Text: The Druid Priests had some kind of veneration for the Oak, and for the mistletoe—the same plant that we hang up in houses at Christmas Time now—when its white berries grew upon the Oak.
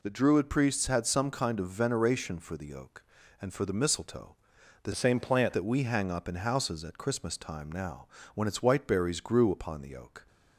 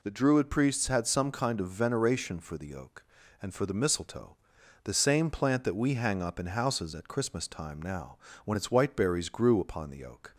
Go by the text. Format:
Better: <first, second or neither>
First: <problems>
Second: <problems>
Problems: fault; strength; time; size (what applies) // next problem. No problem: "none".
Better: second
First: changes voice from "same" to "plant"; from 4.9 to 5.5 s; 0.6 s long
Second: none